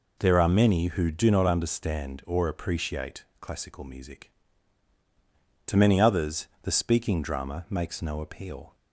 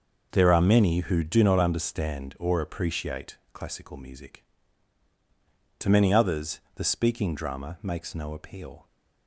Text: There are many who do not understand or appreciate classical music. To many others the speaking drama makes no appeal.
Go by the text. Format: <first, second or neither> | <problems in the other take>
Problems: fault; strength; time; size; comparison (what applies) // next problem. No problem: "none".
first | gets quieter; strong; throughout; 11 dB // pauses between "appreciate" and "classical"; slight; at 3.3 s; 0.16 s long; slight in the first